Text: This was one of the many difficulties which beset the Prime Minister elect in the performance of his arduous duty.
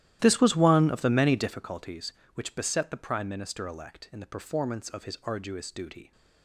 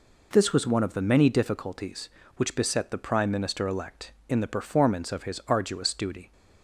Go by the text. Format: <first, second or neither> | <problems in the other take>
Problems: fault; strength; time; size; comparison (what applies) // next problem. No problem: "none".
second | starts louder than the rest; strong; until 1.6 s; 13.5 dB